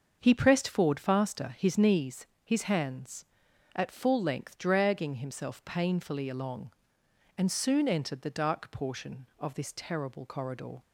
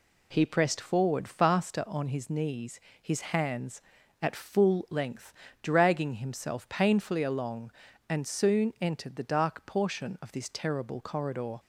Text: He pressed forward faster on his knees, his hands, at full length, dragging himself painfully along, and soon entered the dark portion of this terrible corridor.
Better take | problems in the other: second | starts louder than the rest; until 1.2 s; 6.5 dB // skips "on"; at 1.5 s

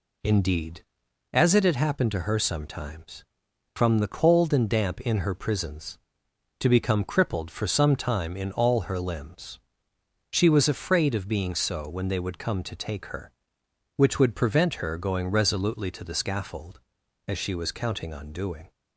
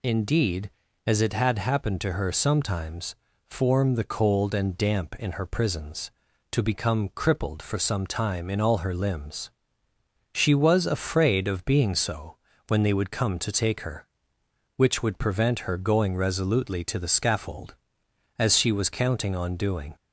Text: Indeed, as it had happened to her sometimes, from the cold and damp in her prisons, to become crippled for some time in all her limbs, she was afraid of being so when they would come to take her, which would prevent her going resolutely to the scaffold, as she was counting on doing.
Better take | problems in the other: first | says "form" for "from"; at 3.4 s // pauses between "so" and "when"; slight; at 12.3 s; 0.32 s long

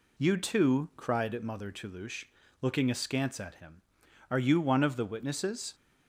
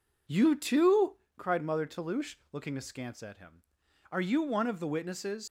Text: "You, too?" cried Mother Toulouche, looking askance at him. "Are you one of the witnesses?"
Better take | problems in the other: first | leaves "witnesses" unfinished; at 5.4 s; 110 ms

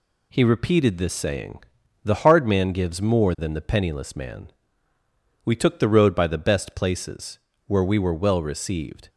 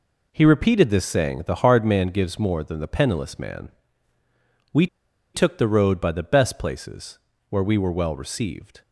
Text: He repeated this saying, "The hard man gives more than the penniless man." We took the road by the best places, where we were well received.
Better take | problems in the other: first | pauses between "We" and "took"; noticeable; at 4.8 s; 0.48 s long

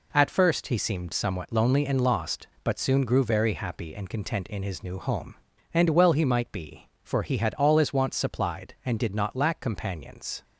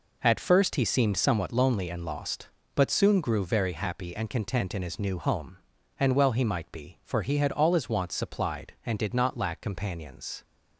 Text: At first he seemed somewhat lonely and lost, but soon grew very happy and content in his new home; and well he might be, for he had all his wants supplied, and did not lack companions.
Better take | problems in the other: neither | none

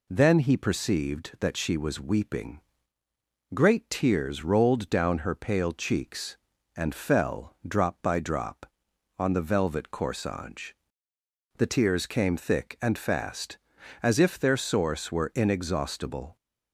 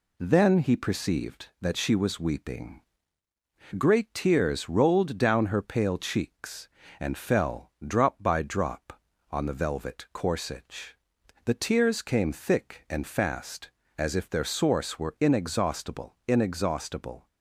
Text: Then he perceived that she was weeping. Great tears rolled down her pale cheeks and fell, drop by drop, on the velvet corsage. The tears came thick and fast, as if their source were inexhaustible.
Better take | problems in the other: first | says "inexhaustible" twice; at 16.2 s

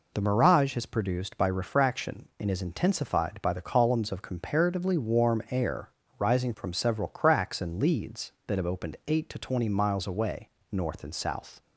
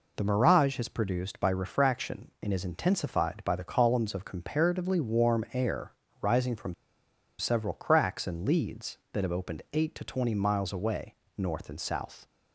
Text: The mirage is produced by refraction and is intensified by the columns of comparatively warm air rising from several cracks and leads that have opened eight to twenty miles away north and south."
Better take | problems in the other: first | pauses between "air" and "rising"; slight; at 5.9 s; 0.30 s long; slight in the first // pauses between "from" and "several"; noticeable; at 6.7 s; 0.66 s long // pauses between "away" and "north"; slight; at 11.1 s; 0.22 s long; slight in the first

